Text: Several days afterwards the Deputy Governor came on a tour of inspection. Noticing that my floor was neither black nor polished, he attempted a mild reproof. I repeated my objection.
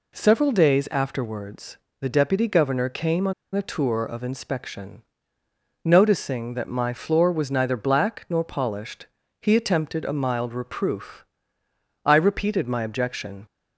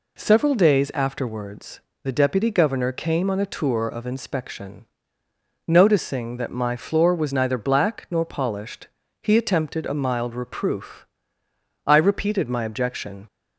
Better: second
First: pauses between "afterwards" and "the"; slight; at 1.7 s; 0.22 s long // pauses between "on" and "a"; slight; at 3.3 s; 0.22 s long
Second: pauses between "afterwards" and "the"; slight; at 1.7 s; 0.22 s long

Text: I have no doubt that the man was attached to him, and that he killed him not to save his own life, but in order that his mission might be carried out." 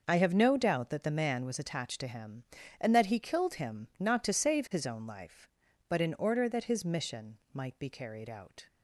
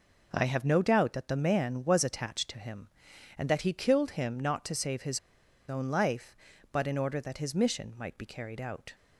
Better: first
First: none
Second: pauses between "his" and "own"; noticeable; at 5.1 s; 0.49 s long

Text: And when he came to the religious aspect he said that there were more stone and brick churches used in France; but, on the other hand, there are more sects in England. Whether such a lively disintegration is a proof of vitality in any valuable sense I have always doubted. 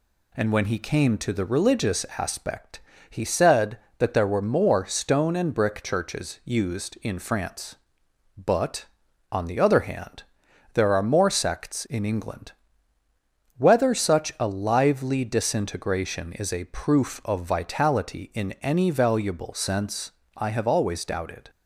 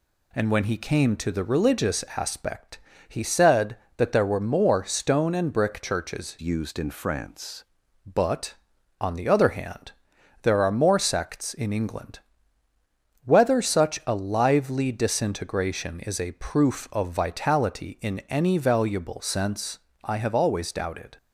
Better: first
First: pauses between "aspect" and "he"; slight; at 2.8 s; 0.30 s long // pauses between "sense" and "I"; slight; at 20.0 s; 0.26 s long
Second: pauses between "aspect" and "he"; slight; at 2.7 s; 0.30 s long // changes voice from "used" to "France"; from 6.4 to 7.6 s; 1.2 s long // pauses between "sense" and "I"; slight; at 19.7 s; 0.26 s long

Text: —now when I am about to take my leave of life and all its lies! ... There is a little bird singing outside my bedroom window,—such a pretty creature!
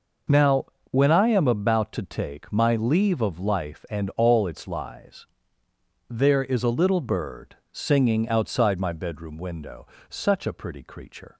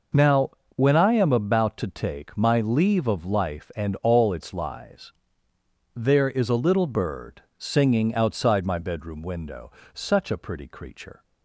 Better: neither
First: pauses between "now" and "when"; slight; at 0.6 s; 0.24 s long // pauses between "bird" and "singing"; slight; at 7.5 s; 0.16 s long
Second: pauses between "now" and "when"; slight; at 0.5 s; 0.24 s long // pauses between "bird" and "singing"; slight; at 7.4 s; 0.16 s long

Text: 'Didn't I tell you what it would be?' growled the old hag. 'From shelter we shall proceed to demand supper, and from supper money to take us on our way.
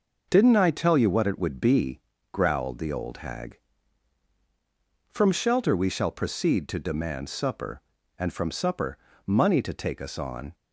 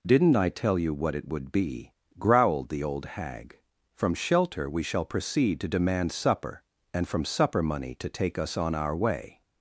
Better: second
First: pauses between "supper" and "money"; slight; at 8.9 s; 0.30 s long // stops before "our way"; at 10.5 s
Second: none

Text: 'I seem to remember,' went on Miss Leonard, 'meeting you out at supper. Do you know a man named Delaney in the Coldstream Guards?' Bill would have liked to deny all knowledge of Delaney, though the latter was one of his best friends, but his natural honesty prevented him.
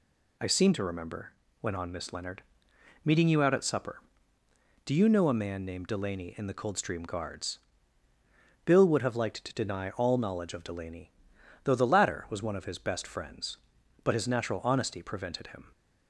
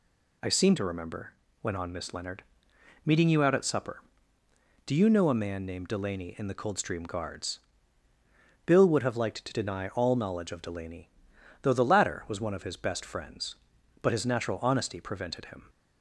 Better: neither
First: none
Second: none

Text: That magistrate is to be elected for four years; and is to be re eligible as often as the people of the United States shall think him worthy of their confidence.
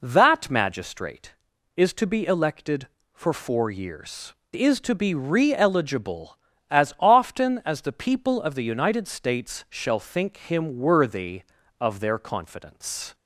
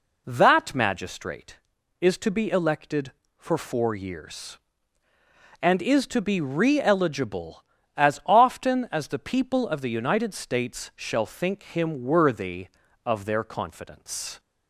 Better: second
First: skips "and"; at 4.4 s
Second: none

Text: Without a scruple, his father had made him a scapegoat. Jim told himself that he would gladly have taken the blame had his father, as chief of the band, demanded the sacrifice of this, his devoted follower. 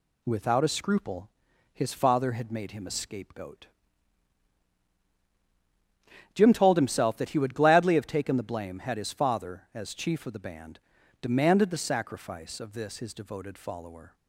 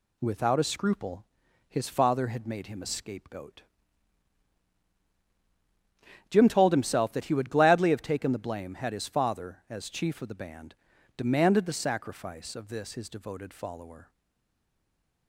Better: first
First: none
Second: stays silent after the last word; noticeable; from 14.0 s on; 1.2 s long

